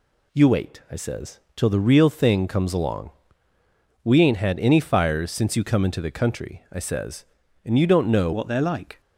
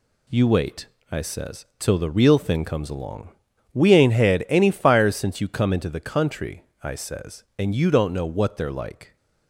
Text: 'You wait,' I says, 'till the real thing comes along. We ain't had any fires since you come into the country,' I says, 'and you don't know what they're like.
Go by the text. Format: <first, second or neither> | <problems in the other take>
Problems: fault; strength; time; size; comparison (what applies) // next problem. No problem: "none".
second | changes voice at "what"; from 8.3 s on; 0.7 s long